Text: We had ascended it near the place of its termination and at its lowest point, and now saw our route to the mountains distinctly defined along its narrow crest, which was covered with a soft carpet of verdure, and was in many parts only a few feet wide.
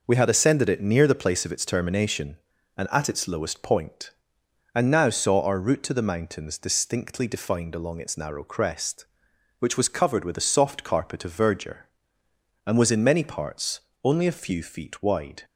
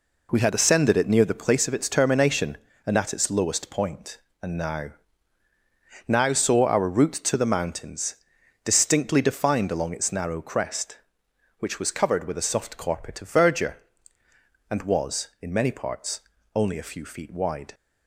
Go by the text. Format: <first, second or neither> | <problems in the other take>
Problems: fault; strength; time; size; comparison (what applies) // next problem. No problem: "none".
first | says "now" twice; at 6.0 s // pauses between "mountains" and "distinctly"; noticeable; at 8.1 s; 0.48 s long // pauses between "parts" and "only"; slight; at 16.1 s; 0.34 s long; slight in the first